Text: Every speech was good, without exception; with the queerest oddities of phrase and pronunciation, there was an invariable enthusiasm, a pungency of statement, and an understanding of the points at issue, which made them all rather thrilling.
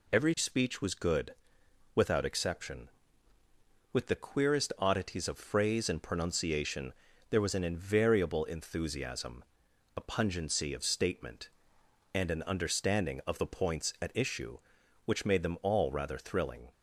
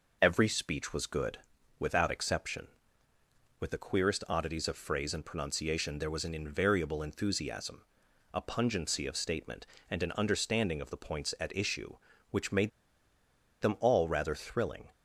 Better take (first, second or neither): first